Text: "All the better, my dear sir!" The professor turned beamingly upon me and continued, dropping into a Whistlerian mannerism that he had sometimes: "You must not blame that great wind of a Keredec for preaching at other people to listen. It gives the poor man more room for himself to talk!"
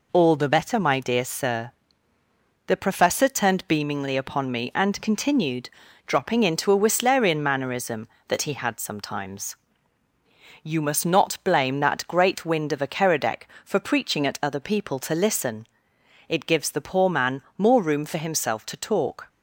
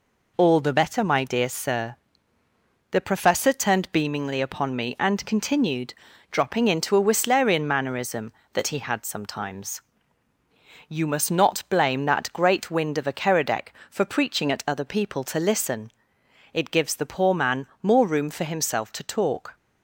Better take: neither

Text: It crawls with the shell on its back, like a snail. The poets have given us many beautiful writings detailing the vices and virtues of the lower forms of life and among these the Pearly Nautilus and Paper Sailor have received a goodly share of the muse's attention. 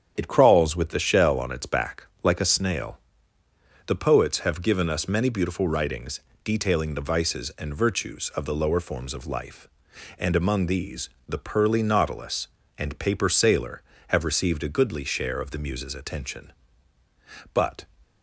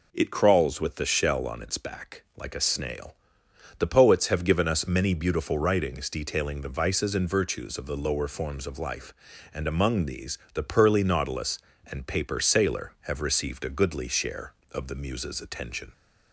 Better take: second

